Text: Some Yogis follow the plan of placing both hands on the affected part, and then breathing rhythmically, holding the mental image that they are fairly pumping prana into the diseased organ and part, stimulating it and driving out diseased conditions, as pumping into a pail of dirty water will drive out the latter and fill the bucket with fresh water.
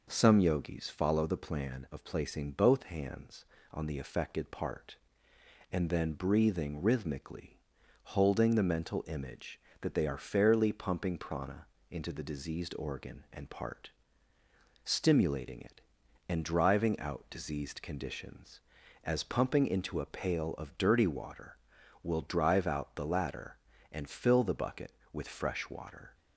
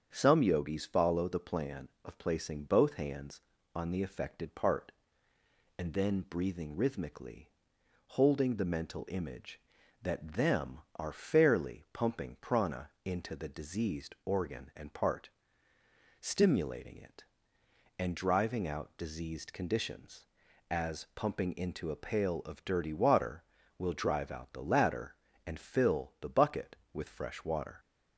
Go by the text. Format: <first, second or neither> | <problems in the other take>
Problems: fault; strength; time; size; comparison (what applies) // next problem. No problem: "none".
first | starts louder than the rest; strong; until 1.1 s; 7 dB // says "them" for "they"; at 10.3 s // pauses between "prana" and "into"; slight; at 12.8 s; 0.16 s long; slight in the first